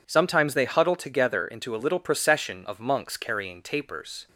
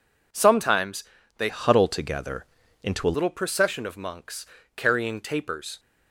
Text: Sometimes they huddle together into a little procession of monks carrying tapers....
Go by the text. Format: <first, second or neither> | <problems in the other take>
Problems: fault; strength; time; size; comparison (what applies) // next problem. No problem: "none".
first | pauses between "Sometimes" and "they"; slight; at 1.0 s; 0.36 s long // changes voice from "huddle" to "a"; from 1.4 to 3.1 s; 1.7 s long // pauses between "together" and "into"; at 2.4 s; 0.40 s long // pauses between "monks" and "carrying"; slight; at 4.4 s; 0.30 s long